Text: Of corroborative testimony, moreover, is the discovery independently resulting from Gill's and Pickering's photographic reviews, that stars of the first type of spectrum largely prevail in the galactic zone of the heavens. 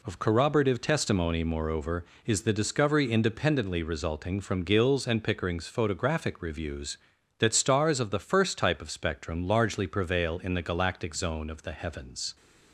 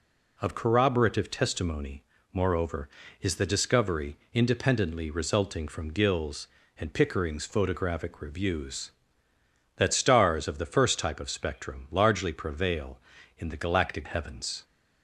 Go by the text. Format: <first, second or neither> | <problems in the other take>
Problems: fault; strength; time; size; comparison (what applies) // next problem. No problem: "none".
first | pauses between "discovery" and "independently"; slight; at 4.1 s; 0.16 s long // skips "zone of the"; at 14.0 s